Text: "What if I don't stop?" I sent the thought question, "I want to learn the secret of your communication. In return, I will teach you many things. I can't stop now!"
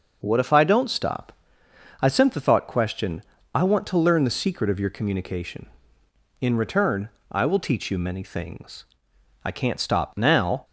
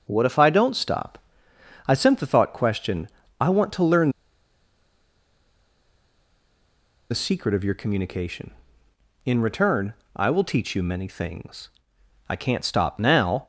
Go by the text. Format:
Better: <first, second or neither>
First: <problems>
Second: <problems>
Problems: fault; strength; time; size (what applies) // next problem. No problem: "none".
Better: first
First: none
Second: pauses between "learn" and "the"; strong; at 4.0 s; 3.0 s long